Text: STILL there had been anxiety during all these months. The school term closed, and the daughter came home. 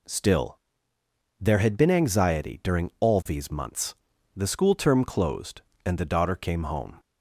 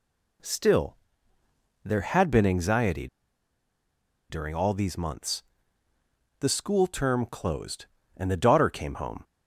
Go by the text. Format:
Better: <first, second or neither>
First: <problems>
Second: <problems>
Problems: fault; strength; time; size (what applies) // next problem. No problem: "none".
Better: first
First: pauses between "STILL" and "there"; noticeable; at 0.5 s; 0.82 s long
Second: pauses between "STILL" and "there"; noticeable; at 0.9 s; 0.86 s long // pauses between "anxiety" and "during"; at 3.0 s; 1.2 s long